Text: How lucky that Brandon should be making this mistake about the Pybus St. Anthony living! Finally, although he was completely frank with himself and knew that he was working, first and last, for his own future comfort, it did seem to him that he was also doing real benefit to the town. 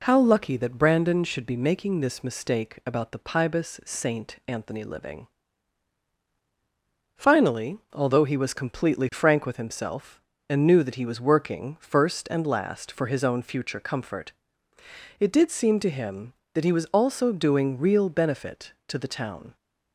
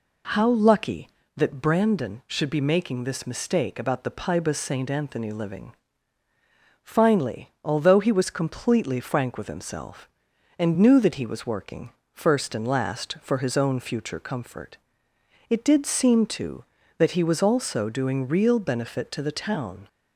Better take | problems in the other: first | skips "him"; at 16.8 s

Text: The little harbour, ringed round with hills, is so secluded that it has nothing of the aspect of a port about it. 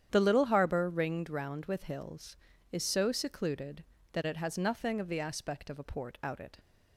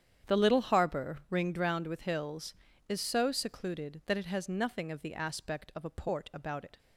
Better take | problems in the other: second | starts louder than the rest; strong; until 1.1 s; 9.5 dB; strong in the second // says "out" for "about"; at 6.2 s

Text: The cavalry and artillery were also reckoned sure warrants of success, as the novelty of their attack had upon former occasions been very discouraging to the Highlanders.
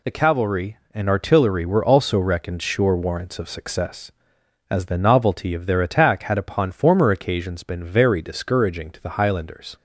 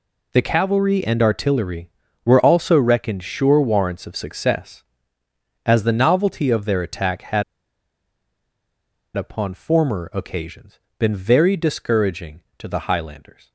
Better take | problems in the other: first | pauses between "had" and "upon"; strong; at 7.4 s; 1.7 s long // pauses between "occasions" and "been"; slight; at 10.7 s; 0.18 s long

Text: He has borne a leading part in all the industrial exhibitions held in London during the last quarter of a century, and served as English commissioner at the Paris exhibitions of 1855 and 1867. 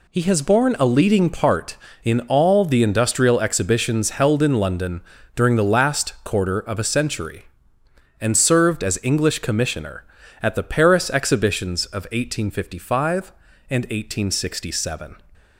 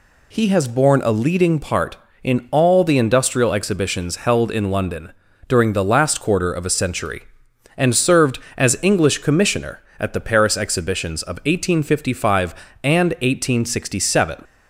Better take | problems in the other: neither | pauses between "London" and "during"; the same in both

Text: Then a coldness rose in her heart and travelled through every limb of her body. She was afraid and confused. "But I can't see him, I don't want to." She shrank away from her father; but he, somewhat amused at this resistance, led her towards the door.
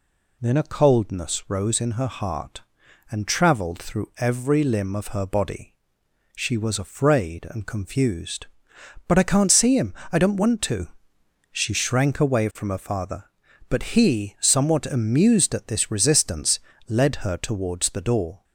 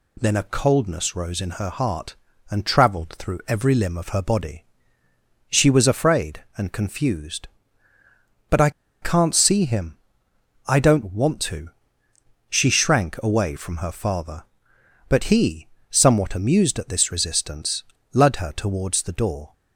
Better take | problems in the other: first | pauses between "I" and "can't"; slight; at 8.7 s; 0.31 s long

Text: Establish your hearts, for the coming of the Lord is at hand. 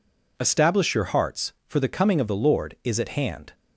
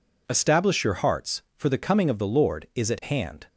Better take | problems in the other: neither | none

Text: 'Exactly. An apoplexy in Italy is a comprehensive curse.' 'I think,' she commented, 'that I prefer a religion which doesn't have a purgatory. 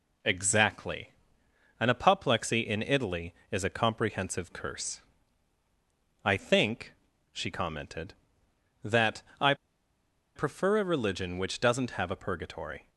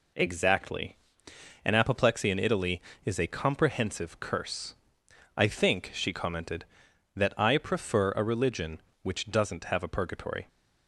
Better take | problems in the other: second | pauses between "that" and "I"; slight; at 9.2 s; 0.18 s long // pauses between "I" and "prefer"; noticeable; at 9.5 s; 0.81 s long

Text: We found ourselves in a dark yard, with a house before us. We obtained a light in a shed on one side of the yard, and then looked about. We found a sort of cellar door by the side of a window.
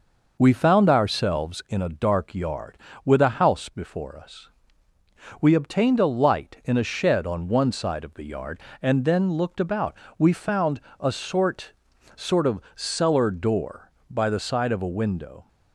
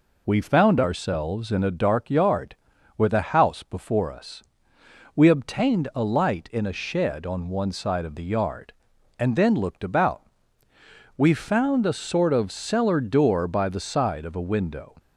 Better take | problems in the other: second | pauses between "found" and "a"; slight; at 10.7 s; 0.20 s long // says "sort" twice; at 12.1 s // pauses between "of" and "cellar"; slight; at 12.5 s; 0.16 s long

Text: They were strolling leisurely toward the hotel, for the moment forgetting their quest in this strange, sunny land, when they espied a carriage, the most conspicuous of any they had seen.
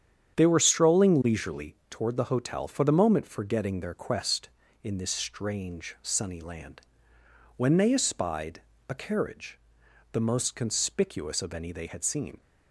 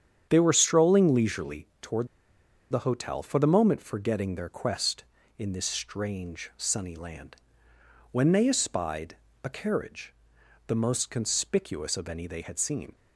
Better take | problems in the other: first | starts louder than the rest; strong; until 1.3 s; 8.5 dB; strong in the first // pauses between "toward" and "the"; noticeable; at 2.0 s; 0.63 s long // pauses between "espied" and "a"; slight; at 9.1 s; 0.28 s long; slight in the first

